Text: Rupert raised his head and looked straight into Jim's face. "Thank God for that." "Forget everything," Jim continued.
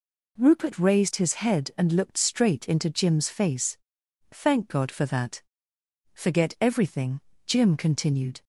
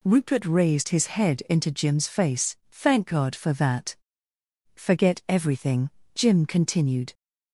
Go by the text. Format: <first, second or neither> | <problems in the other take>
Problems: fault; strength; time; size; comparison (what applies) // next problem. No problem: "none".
first | skips "and looked straight"; at 1.4 s